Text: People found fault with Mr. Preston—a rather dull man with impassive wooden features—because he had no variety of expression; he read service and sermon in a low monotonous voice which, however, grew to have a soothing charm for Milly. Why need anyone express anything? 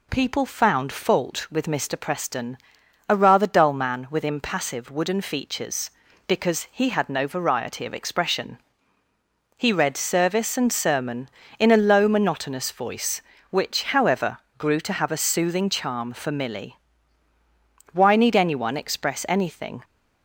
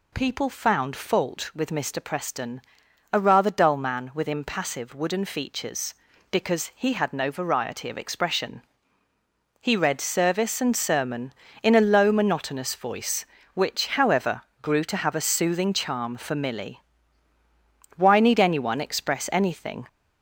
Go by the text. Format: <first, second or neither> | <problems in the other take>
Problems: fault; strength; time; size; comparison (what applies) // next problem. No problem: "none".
first | gets louder; noticeable; throughout; 4 dB